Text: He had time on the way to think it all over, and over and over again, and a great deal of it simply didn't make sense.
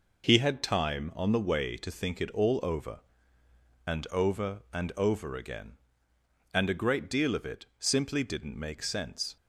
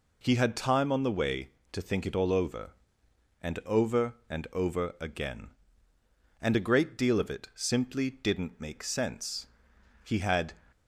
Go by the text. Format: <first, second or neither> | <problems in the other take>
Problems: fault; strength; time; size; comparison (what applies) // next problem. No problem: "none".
first | goes on to say "He had"; from 10.0 s on; 0.50 s long